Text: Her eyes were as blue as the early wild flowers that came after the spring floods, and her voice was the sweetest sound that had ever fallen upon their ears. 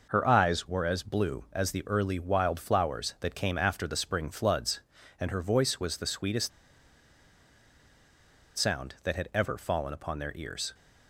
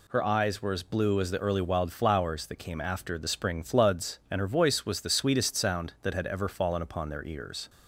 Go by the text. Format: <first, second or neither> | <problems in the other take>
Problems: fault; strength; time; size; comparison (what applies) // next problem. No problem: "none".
second | pauses between "sweetest" and "sound"; strong; at 6.5 s; 2.0 s long